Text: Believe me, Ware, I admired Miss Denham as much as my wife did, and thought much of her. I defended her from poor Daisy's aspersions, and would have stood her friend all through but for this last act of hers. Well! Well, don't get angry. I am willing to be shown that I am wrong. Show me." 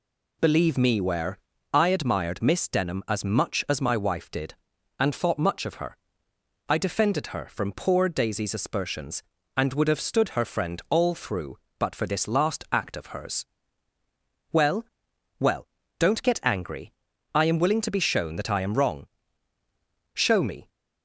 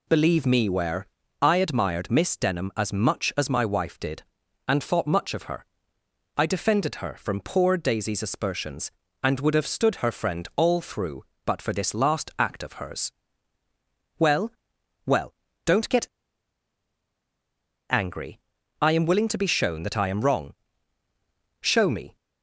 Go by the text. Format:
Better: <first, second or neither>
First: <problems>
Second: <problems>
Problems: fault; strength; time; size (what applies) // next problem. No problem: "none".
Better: first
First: none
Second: pauses between "get" and "angry"; strong; at 16.0 s; 1.8 s long